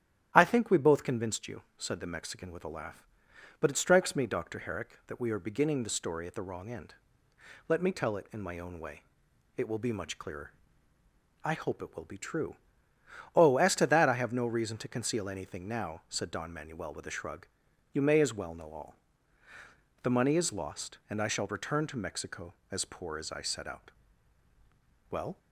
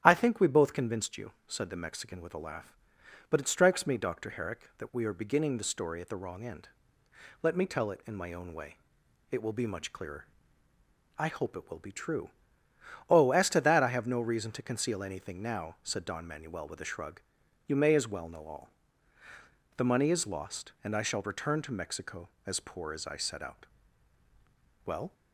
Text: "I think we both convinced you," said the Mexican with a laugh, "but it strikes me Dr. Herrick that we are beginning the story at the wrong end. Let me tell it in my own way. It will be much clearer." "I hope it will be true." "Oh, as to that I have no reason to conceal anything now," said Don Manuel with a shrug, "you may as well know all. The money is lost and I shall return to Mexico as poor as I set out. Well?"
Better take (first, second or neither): neither